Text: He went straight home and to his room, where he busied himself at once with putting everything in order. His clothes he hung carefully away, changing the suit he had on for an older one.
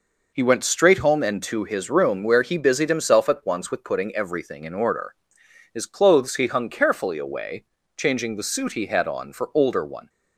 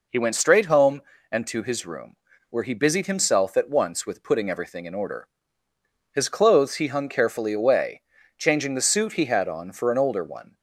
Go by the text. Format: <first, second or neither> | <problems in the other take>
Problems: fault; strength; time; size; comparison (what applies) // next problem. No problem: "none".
second | skips "an"; at 9.5 s